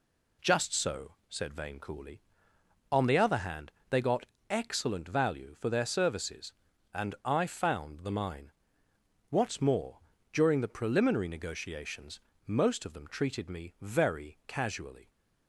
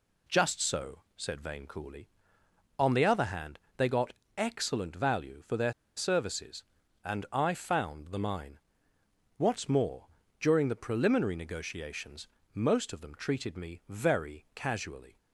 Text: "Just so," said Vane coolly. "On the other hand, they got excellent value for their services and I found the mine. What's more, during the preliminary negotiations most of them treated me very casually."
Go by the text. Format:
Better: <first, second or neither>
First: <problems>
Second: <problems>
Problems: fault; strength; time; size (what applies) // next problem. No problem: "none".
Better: first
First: pauses between "got" and "excellent"; slight; at 4.2 s; 0.22 s long // pauses between "negotiations" and "most"; slight; at 12.1 s; 0.26 s long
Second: pauses between "got" and "excellent"; slight; at 4.1 s; 0.22 s long // pauses between "their" and "services"; slight; at 5.7 s; 0.23 s long // pauses between "negotiations" and "most"; slight; at 12.2 s; 0.26 s long